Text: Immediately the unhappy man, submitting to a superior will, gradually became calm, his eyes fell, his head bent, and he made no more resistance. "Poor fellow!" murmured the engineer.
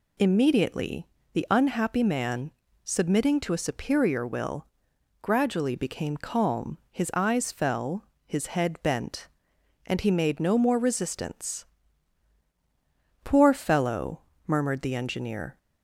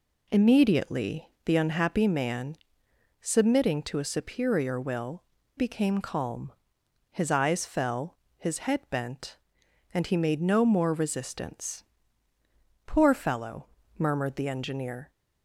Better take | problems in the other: first | pauses between "Immediately" and "the"; slight; at 1.2 s; 0.16 s long; slight in the first // skips "gradually"; at 5.3 s

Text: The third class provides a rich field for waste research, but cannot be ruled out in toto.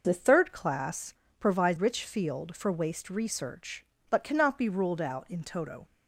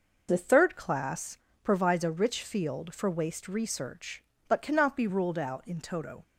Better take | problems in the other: second | pauses between "class" and "provides"; slight; at 1.1 s; 0.26 s long; slight in the second // skips "a"; at 1.7 s

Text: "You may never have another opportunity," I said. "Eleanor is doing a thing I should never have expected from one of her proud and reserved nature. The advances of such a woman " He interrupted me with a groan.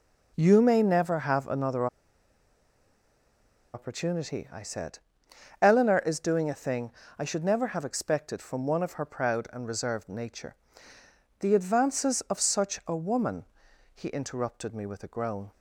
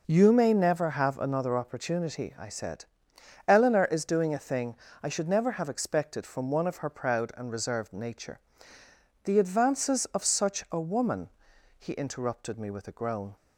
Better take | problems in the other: second | pauses between "another" and "opportunity"; strong; at 1.8 s; 1.8 s long // pauses between "thing" and "I"; slight; at 6.9 s; 0.26 s long; slight in the second

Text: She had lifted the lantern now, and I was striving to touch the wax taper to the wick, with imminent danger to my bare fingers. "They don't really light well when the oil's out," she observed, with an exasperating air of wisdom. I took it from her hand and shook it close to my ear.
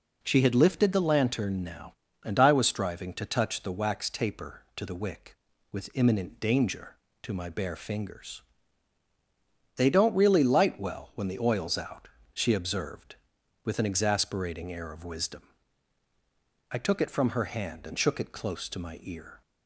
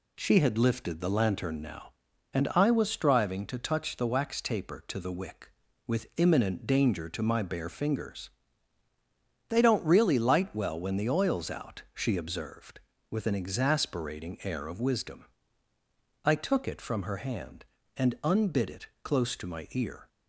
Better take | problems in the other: first | says "unbid" for "shook"; at 18.2 s

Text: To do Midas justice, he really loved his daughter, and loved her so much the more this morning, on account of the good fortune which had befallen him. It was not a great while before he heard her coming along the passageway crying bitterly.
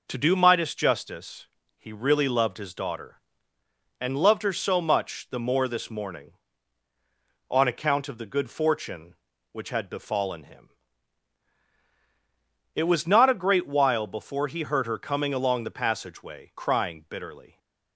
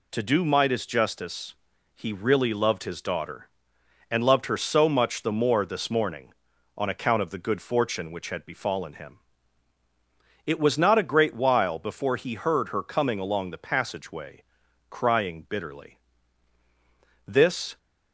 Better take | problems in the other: first | pauses between "passageway" and "crying"; noticeable; at 14.4 s; 0.46 s long // goes on to say "This"; from 17.2 s on; 0.52 s long

